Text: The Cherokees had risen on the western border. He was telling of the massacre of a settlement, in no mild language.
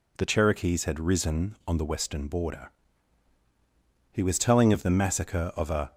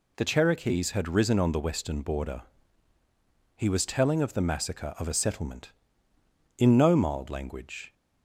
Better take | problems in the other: second | stops before "settlement in no mild language"; at 5.9 s

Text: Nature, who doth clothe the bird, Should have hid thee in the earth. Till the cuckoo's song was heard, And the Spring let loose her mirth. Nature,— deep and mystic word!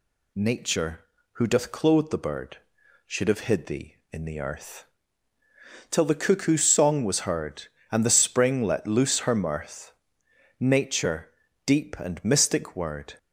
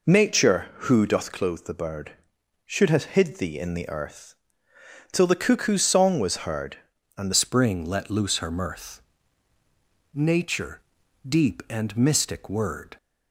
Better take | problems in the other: first | changes voice at "Spring"; from 7.3 s on; 5.6 s long

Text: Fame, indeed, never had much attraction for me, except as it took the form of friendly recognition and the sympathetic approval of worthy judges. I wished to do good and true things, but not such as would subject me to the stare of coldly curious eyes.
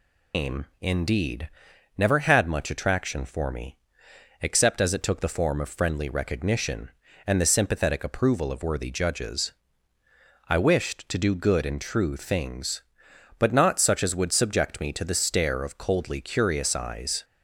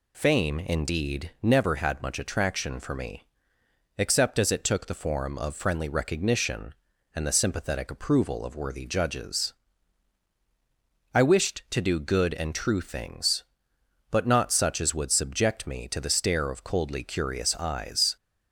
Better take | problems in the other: second | loses the start of "Fame"; at 0.3 s; 205 ms

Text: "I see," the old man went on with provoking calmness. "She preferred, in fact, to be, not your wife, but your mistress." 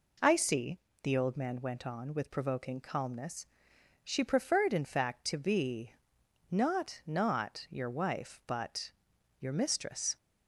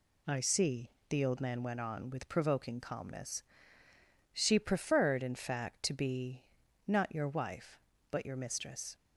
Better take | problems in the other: second | says "not" twice; at 7.0 s // pauses between "but" and "your"; noticeable; at 8.9 s; 0.48 s long

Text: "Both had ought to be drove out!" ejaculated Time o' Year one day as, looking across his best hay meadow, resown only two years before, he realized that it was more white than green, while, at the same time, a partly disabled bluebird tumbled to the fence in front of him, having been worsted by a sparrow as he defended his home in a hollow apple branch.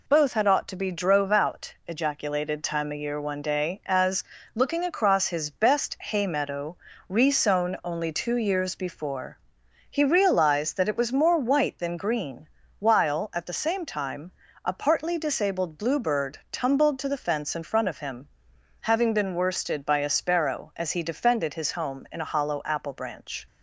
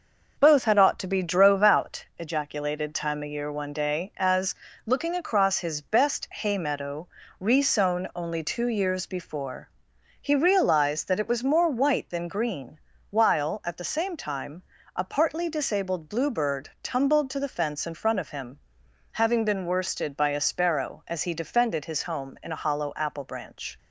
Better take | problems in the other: first | starts louder than the rest; noticeable; until 2.1 s; 6 dB

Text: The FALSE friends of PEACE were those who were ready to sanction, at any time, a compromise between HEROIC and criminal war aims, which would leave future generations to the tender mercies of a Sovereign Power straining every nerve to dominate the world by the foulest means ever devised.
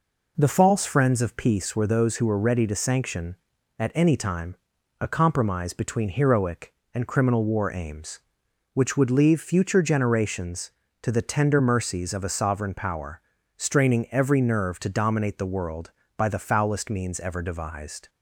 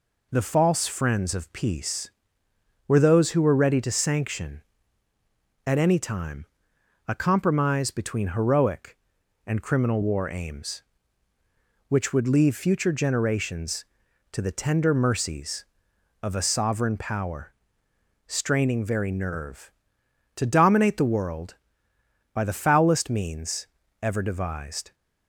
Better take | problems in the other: first | pauses between "Power" and "straining"; noticeable; at 17.5 s; 0.72 s long; slight in the first // says "very" for "every"; at 18.8 s // pauses between "means" and "ever"; slight; at 23.6 s; 0.34 s long

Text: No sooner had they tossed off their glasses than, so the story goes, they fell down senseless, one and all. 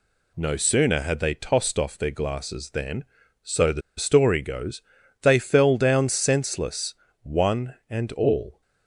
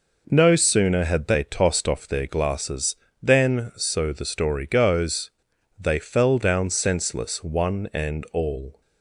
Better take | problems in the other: second | pauses between "the" and "story"; slight; at 3.8 s; 0.17 s long

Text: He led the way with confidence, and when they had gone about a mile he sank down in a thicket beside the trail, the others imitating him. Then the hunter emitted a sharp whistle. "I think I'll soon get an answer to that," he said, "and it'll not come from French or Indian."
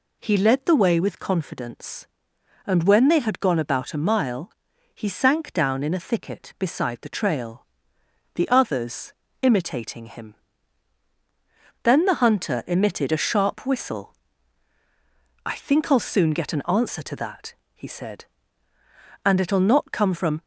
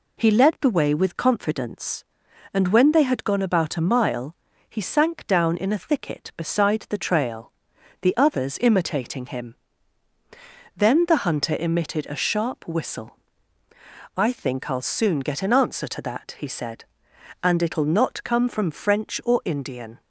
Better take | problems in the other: second | pauses between "mile" and "he"; at 4.5 s; 0.42 s long; slight in the second // pauses between "others" and "imitating"; slight; at 9.1 s; 0.26 s long // stops before "French or Indian"; at 20.4 s

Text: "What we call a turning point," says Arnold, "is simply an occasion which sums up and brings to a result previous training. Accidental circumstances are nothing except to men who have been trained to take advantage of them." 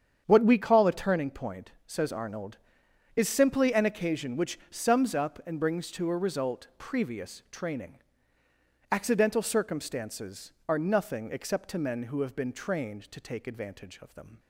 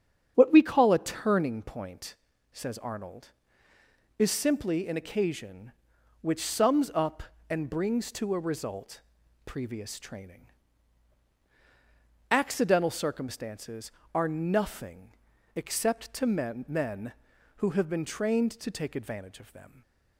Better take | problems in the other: first | starts louder than the rest; strong; until 1.3 s; 8.5 dB; strong in the first // pauses between "result" and "previous"; at 9.0 s; 0.44 s long // pauses between "nothing" and "except"; at 15.1 s; 0.40 s long // says "men" twice; at 16.6 s // stays silent after the last word; slight; from 19.6 s on; 0.5 s long

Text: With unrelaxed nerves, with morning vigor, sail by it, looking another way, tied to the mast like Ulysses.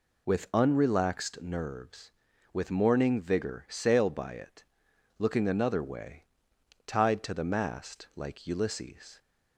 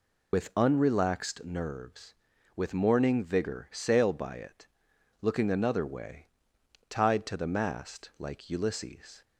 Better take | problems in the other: first | loses the start of "With"; at 0.3 s; 35 ms

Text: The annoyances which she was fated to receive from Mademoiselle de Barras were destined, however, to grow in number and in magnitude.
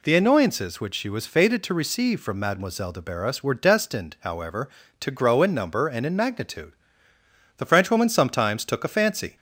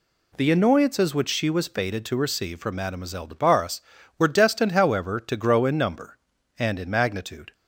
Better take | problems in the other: second | goes on to say "The Frenchwoman sometimes took a fancy"; strong; from 7.5 s on; 1.7 s long

